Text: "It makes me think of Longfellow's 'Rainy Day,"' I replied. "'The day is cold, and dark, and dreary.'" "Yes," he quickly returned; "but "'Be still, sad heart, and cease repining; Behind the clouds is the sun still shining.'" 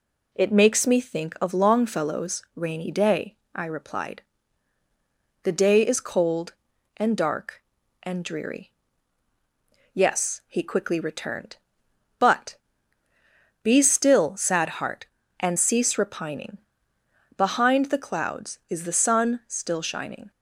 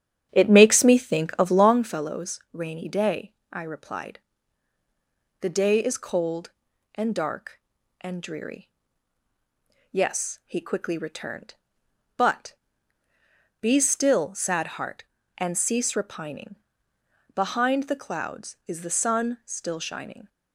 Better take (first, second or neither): first